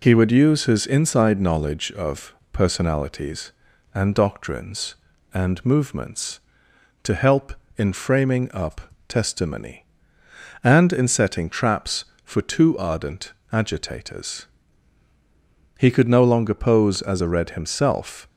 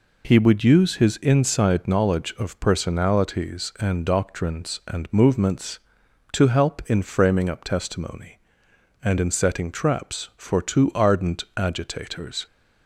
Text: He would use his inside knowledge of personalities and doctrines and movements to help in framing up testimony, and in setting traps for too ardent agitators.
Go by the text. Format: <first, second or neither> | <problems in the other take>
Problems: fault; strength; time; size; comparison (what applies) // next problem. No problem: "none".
second | pauses between "of" and "personalities"; slight; at 2.3 s; 0.16 s long // pauses between "up" and "testimony"; slight; at 8.8 s; 0.26 s long // pauses between "ardent" and "agitators"; slight; at 13.3 s; 0.22 s long // goes on to say "He could no longer pose as a Red himself"; strong; from 15.7 s on; 2.4 s long